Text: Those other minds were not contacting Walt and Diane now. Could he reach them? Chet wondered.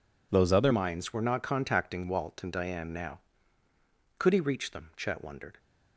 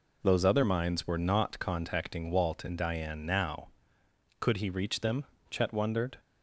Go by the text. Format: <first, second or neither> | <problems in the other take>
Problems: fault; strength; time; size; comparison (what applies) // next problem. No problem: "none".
second | changes voice at "minds"; from 0.7 s on; 4.8 s long